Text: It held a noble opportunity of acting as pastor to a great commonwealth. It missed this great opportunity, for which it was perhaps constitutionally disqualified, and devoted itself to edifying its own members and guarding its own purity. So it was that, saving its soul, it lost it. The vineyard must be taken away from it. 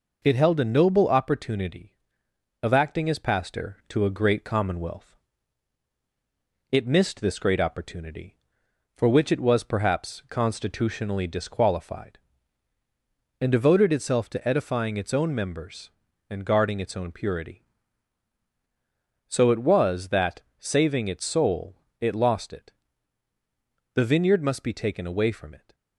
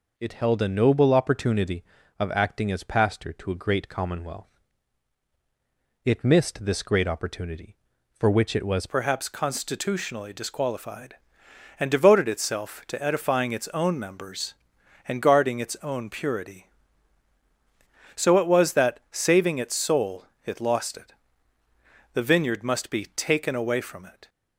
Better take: first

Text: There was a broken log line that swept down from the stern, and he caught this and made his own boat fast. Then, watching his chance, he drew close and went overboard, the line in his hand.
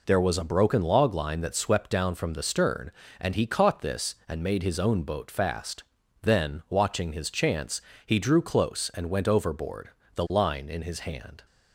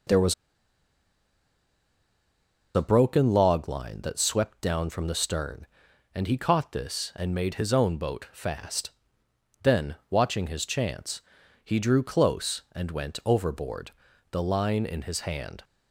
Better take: first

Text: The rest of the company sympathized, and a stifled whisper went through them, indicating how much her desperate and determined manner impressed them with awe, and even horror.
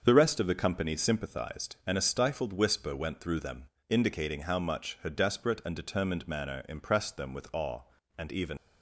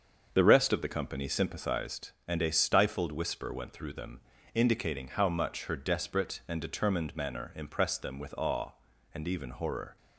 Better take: second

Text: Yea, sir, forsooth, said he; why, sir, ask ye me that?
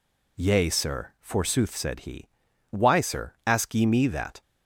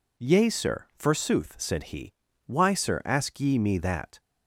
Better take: neither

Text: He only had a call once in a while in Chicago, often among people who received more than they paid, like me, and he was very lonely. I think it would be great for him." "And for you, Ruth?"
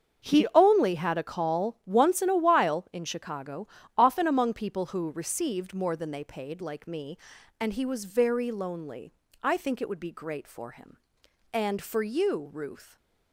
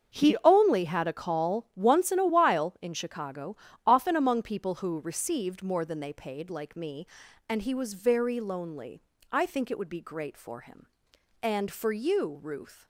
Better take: neither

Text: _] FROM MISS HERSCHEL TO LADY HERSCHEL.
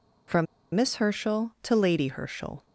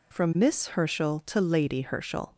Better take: second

